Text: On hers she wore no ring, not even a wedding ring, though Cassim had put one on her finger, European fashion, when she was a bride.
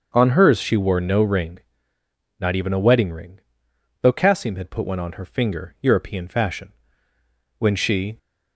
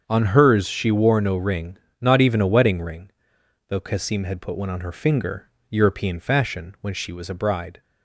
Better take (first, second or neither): second